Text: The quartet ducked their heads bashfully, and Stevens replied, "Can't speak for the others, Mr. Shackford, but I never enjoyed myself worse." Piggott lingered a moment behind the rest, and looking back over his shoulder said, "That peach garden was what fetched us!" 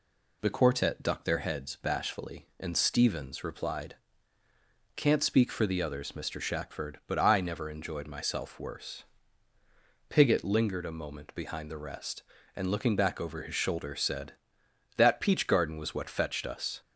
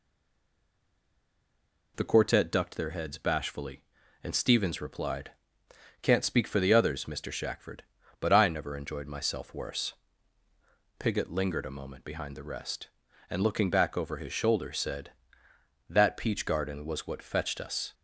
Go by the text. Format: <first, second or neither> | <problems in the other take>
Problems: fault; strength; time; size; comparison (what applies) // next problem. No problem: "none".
first | stays silent before the first word; noticeable; until 1.9 s; 1.9 s long